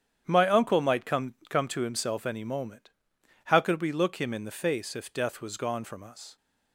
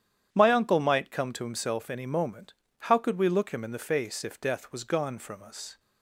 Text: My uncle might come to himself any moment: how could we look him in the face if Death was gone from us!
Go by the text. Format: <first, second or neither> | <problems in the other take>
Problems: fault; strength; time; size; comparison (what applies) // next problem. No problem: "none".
second | starts louder than the rest; strong; until 1.2 s; 9 dB; strong in the second // says "come" twice; at 1.5 s